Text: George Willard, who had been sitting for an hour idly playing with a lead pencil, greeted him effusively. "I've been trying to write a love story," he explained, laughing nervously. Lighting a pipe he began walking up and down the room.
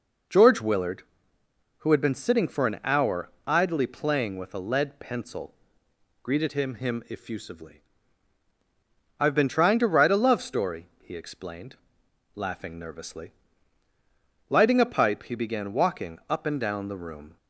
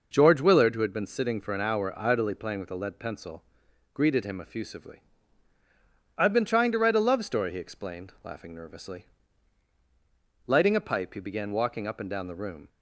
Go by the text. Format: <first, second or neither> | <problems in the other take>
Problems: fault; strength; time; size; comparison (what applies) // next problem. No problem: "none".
second | pauses between "hour" and "idly"; slight; at 3.3 s; 0.16 s long // says "him" twice; at 6.7 s